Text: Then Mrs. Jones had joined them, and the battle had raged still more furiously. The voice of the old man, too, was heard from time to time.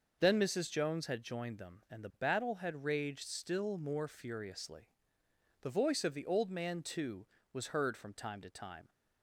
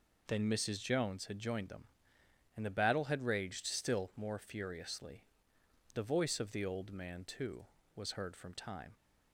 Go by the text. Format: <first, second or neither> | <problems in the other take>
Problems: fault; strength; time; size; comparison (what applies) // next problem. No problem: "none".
first | stops before "to time"; at 8.9 s